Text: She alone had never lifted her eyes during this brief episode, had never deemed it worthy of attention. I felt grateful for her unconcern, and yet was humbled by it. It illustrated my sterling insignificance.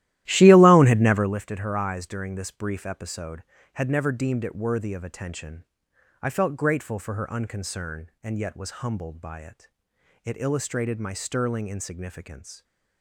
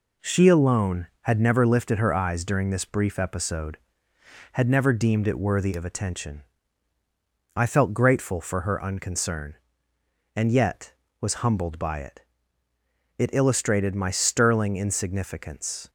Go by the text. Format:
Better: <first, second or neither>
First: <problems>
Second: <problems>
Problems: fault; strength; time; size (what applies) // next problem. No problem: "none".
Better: second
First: starts louder than the rest; strong; until 1.4 s; 14.5 dB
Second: none